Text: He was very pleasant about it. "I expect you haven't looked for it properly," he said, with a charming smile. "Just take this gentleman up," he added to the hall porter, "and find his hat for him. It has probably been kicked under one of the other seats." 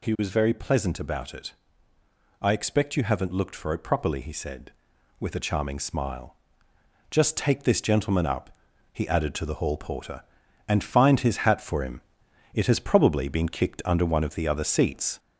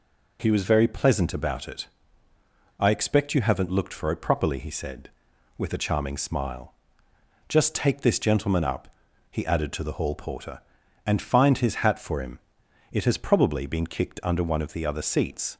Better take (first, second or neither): second